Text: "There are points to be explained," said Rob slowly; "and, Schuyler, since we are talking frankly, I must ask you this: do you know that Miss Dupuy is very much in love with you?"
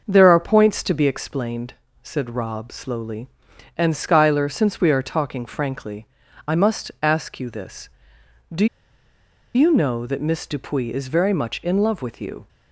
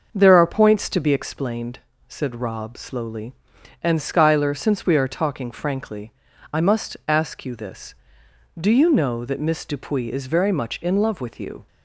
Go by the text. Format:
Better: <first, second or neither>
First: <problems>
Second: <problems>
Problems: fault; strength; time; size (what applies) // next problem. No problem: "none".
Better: second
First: starts louder than the rest; until 1.0 s; 6 dB // pauses between "do" and "you"; noticeable; at 8.6 s; 0.89 s long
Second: starts louder than the rest; until 1.1 s; 6 dB